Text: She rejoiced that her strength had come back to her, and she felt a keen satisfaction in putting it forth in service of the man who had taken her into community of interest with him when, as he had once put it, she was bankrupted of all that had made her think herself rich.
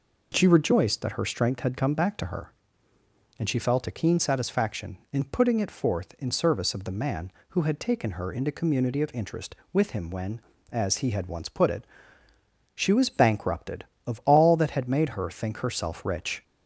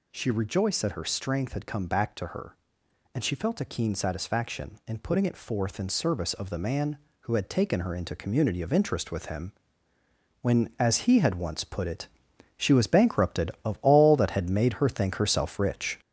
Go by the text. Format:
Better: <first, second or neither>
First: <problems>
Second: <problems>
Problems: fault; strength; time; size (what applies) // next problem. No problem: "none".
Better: first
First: none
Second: gets louder; noticeable; throughout; 5 dB // pauses between "him" and "when"; noticeable; at 9.5 s; 0.90 s long